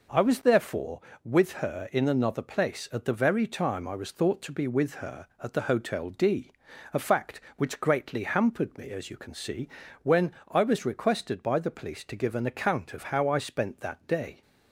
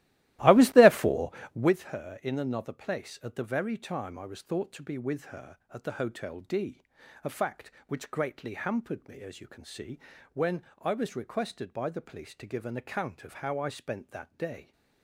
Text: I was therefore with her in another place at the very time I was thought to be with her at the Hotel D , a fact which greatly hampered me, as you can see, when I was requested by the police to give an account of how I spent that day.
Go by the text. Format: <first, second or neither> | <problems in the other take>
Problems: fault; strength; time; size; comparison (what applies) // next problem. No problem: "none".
first | starts louder than the rest; strong; until 1.8 s; 16 dB